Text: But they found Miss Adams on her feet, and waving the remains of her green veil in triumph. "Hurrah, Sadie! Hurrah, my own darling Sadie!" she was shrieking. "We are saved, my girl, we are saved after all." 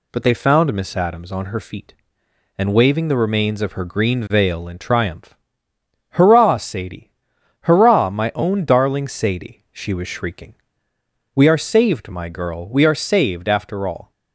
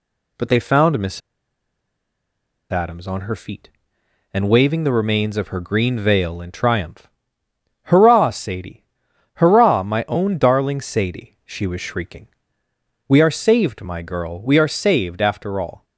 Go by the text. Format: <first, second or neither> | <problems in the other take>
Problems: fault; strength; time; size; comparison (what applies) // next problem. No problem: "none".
first | pauses between "Miss" and "Adams"; strong; at 1.2 s; 1.5 s long